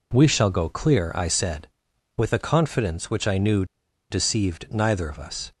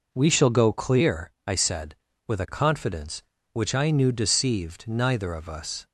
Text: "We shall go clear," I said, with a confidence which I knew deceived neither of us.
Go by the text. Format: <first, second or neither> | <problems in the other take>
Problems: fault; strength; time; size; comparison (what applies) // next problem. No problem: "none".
second | pauses between "knew" and "deceived"; noticeable; at 3.6 s; 0.46 s long